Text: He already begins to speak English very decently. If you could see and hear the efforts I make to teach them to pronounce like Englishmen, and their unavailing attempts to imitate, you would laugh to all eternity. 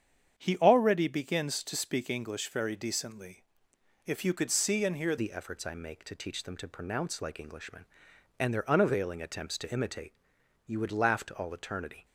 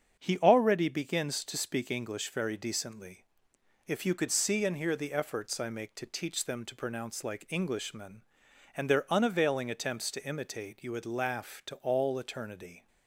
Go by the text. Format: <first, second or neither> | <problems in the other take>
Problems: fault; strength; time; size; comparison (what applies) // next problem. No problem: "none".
second | starts louder than the rest; strong; until 1.4 s; 8 dB; strong in the second // changes voice at "the"; from 5.1 s on; 6.9 s long